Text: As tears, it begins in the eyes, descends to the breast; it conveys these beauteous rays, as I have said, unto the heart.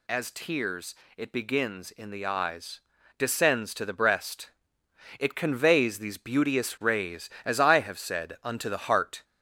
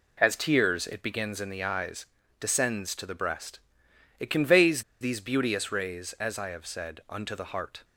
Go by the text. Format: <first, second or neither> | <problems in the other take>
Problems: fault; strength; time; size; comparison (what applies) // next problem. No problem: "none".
first | pauses between "conveys" and "these"; slight; at 4.8 s; 0.18 s long